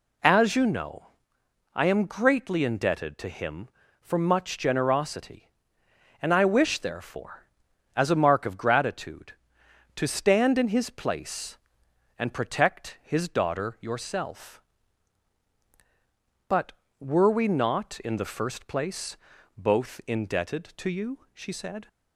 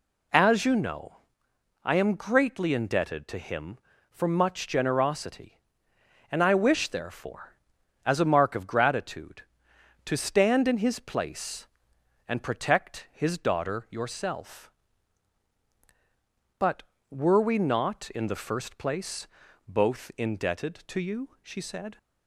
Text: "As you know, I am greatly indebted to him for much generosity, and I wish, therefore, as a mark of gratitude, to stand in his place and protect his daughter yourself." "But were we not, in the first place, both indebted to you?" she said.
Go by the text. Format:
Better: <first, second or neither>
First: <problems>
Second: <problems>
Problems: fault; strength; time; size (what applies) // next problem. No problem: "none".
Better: neither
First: none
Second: none